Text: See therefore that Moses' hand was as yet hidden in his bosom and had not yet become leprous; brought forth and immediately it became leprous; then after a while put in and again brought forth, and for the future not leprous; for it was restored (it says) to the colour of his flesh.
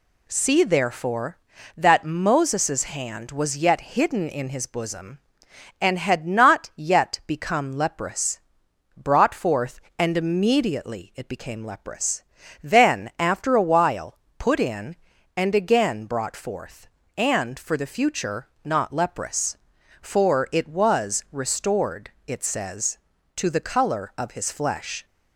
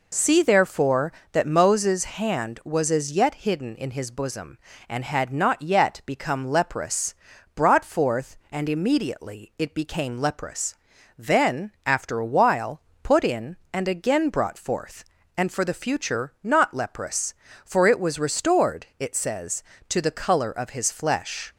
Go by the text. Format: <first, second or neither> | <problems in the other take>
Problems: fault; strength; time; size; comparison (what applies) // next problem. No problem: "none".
second | skips "as"; at 3.5 s // pauses between "while" and "put"; slight; at 14.1 s; 0.20 s long; slight in the second // pauses between "future" and "not"; slight; at 18.4 s; 0.18 s long